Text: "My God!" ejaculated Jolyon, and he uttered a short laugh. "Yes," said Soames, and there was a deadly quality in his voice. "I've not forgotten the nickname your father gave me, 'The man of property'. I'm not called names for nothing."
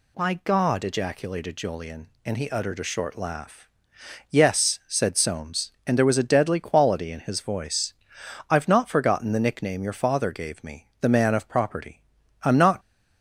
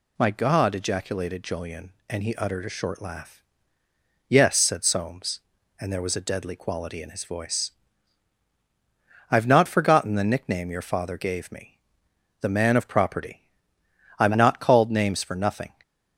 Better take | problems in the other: second | stops before "called names for nothing"; at 12.7 s

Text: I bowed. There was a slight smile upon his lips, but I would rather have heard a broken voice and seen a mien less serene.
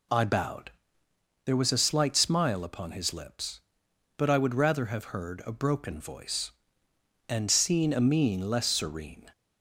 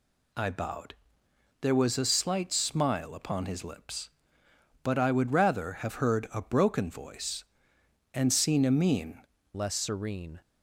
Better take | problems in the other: first | changes voice at "less"; from 9.5 s on; 0.9 s long

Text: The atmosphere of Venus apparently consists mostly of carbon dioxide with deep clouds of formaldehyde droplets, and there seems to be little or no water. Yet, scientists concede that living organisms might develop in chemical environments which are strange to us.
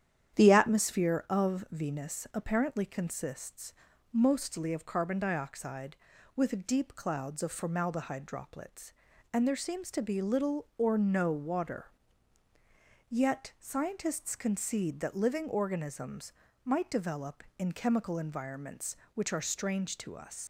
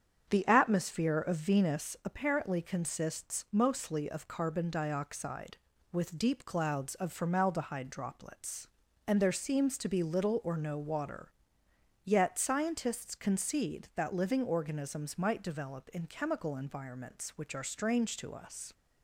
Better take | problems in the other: second | starts louder than the rest; strong; until 1.4 s; 10 dB; strong in the second // pauses between "consists" and "mostly"; at 3.7 s; 0.40 s long // pauses between "organisms" and "might"; slight; at 16.3 s; 0.34 s long // leaves "us" unfinished; at 20.4 s; 85 ms

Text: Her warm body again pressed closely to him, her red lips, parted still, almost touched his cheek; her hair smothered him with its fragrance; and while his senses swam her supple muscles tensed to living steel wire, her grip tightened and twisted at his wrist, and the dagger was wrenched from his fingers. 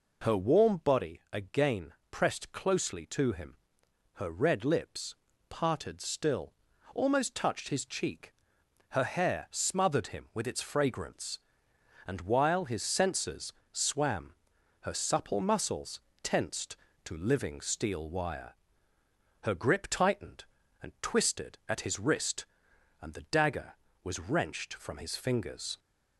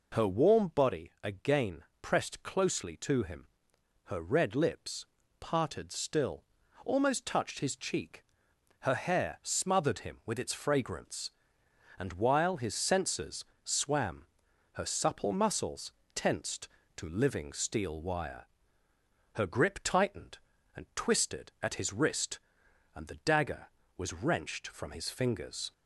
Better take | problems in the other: neither | pauses between "again" and "pressed"; slight; the same in both // pauses between "senses" and "swam"; slight; the same in both // pauses between "swam" and "her"; noticeable; the same in both // pauses between "muscles" and "tensed"; slight; the same in both

